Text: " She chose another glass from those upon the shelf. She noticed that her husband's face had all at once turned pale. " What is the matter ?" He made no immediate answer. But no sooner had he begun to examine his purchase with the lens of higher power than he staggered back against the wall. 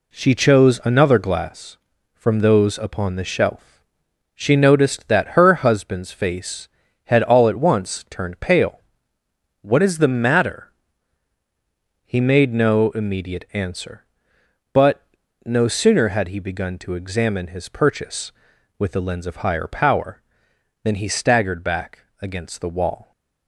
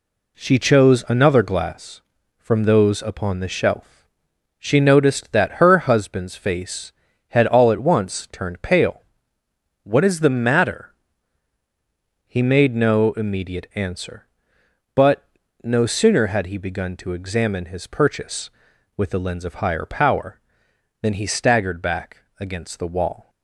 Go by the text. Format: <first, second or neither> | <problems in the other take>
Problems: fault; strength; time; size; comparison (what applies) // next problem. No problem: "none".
neither | pauses between "But" and "no"; the same in both // pauses between "back" and "against"; slight; the same in both